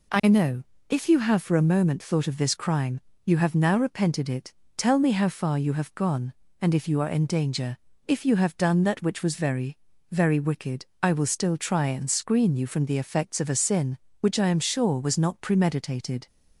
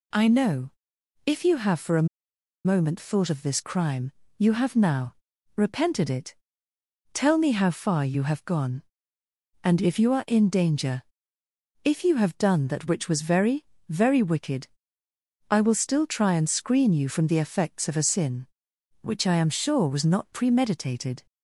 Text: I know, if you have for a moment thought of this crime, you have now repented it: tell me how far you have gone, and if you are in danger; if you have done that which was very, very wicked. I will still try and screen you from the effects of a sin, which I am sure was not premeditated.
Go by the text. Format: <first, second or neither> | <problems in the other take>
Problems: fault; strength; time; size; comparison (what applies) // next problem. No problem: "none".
first | pauses between "a" and "moment"; noticeable; at 2.0 s; 0.57 s long // pauses between "now" and "repented"; at 5.1 s; 0.42 s long